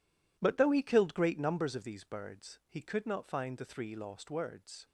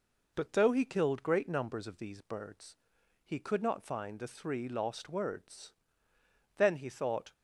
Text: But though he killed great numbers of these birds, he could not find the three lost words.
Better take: first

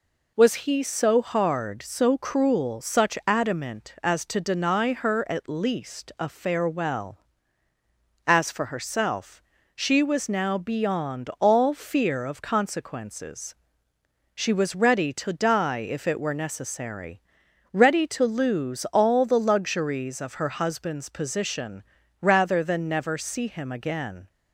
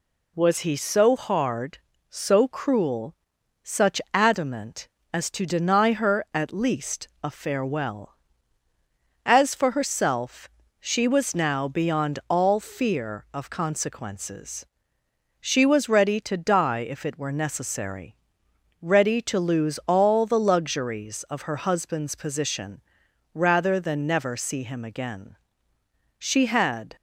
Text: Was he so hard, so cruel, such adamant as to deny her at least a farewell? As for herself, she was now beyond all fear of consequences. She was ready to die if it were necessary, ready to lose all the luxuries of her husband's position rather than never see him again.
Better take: first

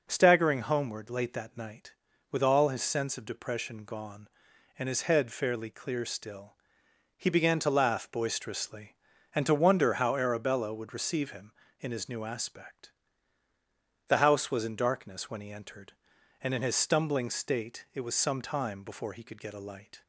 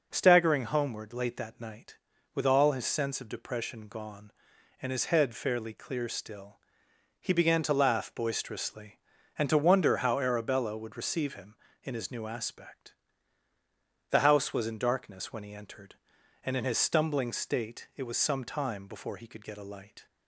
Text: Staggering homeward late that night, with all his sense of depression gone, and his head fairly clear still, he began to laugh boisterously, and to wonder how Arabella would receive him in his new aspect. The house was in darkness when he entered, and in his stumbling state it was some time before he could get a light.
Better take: neither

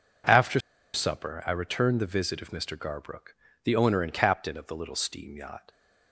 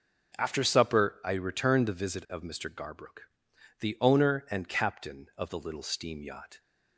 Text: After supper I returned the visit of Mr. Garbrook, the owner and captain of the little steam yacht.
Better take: second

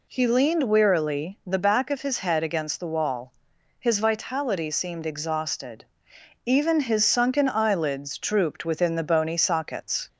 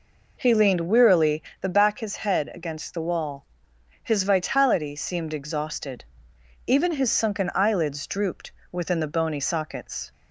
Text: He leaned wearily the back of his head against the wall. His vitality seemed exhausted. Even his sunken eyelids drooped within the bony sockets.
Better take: first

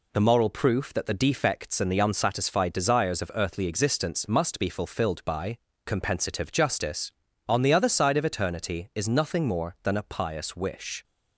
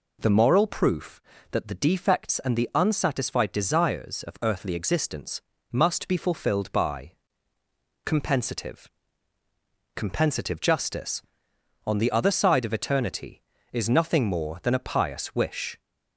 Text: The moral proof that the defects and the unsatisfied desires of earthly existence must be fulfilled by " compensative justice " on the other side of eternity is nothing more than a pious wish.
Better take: first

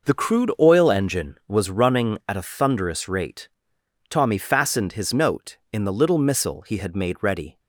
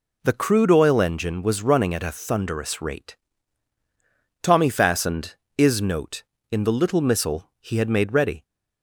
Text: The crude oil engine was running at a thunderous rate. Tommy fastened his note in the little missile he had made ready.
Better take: first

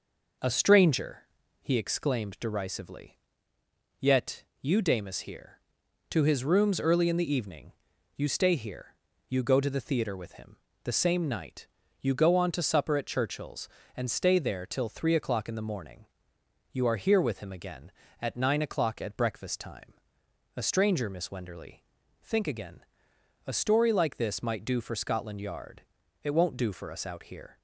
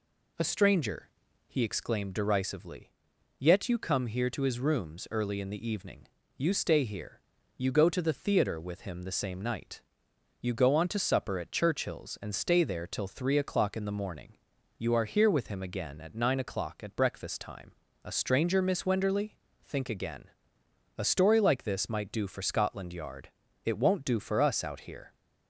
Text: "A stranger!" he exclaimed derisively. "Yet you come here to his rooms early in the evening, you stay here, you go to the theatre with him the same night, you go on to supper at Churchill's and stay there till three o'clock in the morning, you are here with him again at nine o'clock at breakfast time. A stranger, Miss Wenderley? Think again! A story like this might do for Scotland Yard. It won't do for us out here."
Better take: second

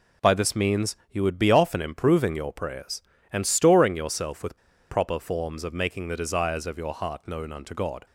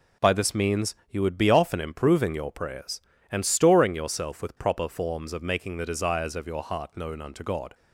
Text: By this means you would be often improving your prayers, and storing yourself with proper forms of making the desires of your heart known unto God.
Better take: second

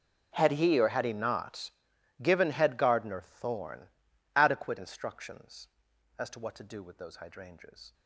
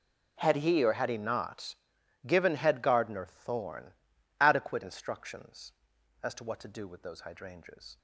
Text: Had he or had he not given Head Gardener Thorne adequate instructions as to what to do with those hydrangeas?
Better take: second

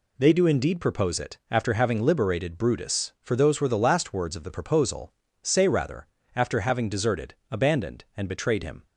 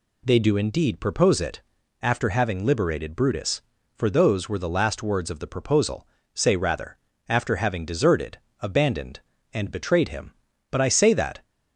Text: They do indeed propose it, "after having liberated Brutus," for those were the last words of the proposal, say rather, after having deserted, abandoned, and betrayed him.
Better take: first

